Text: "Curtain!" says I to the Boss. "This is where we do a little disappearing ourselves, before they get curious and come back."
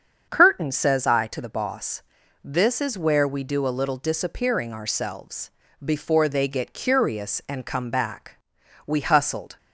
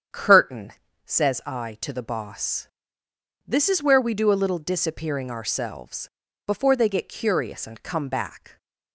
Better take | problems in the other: second | starts louder than the rest; strong; until 1.3 s; 7 dB; strong in the second // goes on to say "We hustled"; noticeable; from 8.8 s on; 0.72 s long

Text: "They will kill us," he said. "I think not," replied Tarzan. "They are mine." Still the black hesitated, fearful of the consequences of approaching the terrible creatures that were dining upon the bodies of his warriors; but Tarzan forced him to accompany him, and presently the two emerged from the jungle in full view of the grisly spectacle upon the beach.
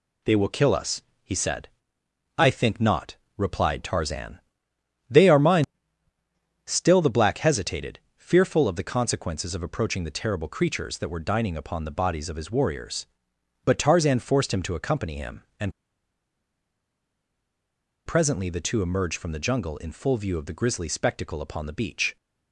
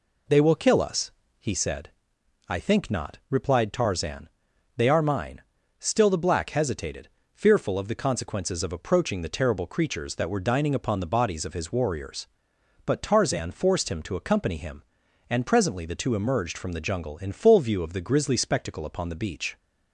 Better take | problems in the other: second | pauses between "and" and "presently"; strong; at 15.7 s; 2.3 s long

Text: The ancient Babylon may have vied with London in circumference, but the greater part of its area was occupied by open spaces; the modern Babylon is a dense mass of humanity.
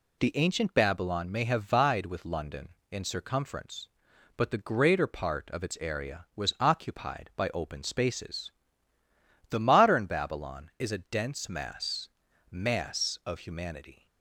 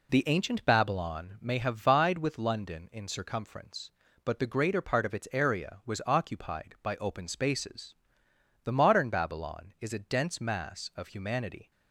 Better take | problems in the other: second | says "mass" twice; at 12.5 s

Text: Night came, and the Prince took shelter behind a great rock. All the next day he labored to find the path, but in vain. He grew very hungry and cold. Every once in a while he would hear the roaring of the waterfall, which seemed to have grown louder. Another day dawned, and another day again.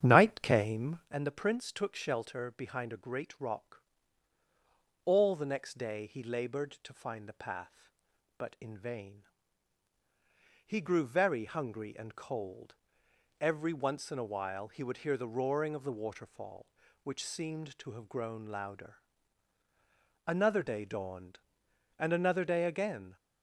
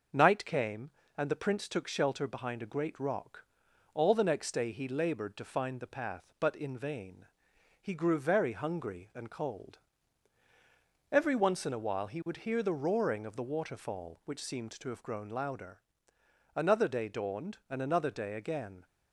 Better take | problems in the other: second | starts louder than the rest; strong; until 1.1 s; 9 dB

